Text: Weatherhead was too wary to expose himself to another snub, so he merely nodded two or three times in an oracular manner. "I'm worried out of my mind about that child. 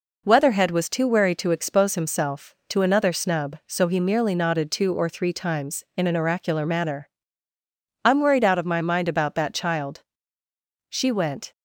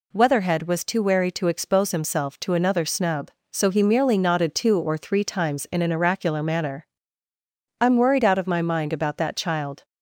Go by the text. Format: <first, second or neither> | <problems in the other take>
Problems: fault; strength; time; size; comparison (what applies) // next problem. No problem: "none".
second | goes on to say "She went"; noticeable; from 10.8 s on; 0.64 s long